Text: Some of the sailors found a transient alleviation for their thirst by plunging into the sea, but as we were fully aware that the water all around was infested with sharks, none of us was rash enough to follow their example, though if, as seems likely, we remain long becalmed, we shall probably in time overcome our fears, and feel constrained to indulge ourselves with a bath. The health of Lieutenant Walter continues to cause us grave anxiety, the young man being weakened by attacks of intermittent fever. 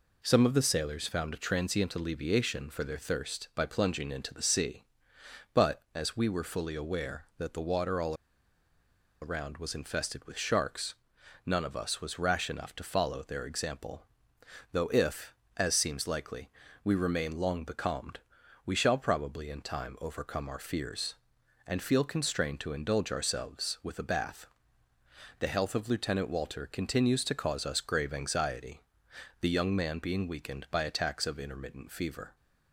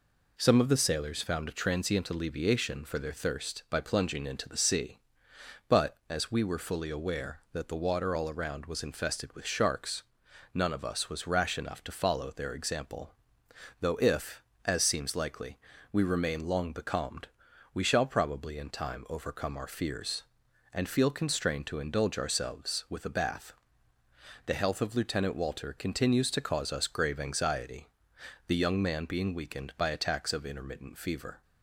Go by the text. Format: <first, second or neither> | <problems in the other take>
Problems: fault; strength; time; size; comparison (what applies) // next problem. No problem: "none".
second | pauses between "all" and "around"; at 8.1 s; 1.0 s long